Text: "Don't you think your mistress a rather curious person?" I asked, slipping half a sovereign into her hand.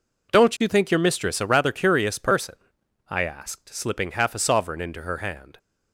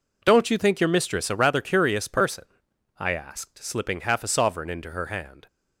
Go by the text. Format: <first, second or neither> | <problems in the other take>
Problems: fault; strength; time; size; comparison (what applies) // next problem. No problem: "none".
neither | none